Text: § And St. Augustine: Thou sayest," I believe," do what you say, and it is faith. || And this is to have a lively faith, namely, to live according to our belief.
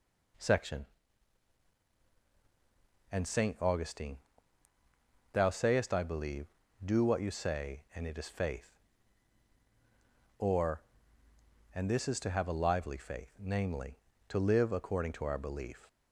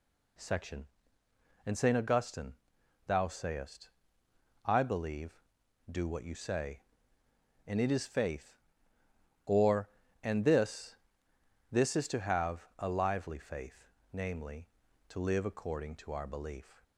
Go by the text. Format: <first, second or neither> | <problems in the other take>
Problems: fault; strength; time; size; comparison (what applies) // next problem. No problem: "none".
first | says "this" twice; at 11.7 s